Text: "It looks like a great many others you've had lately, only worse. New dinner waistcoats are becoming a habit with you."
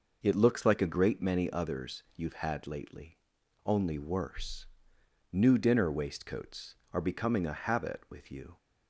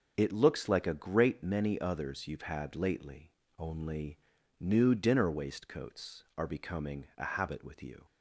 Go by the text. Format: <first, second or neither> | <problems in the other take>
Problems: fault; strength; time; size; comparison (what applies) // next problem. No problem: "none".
first | skips "worse"; at 4.3 s